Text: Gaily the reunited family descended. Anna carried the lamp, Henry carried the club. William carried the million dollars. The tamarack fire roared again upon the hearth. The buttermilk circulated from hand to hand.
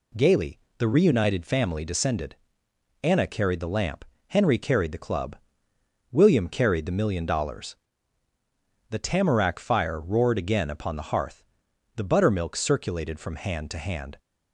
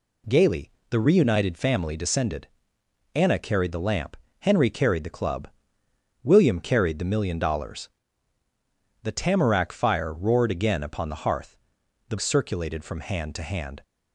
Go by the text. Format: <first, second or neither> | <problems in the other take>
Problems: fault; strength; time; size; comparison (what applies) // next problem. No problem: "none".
first | pauses between "Gaily" and "the"; slight; at 0.7 s; 0.18 s long; slight in the first // skips "buttermilk"; at 12.1 s